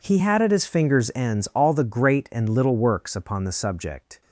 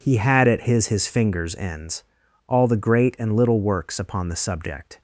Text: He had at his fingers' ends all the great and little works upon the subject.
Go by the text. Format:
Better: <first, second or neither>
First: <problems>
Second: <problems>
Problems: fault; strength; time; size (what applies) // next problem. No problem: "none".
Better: first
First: none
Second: says "his" twice; at 0.8 s // pauses between "ends" and "all"; noticeable; at 2.0 s; 0.46 s long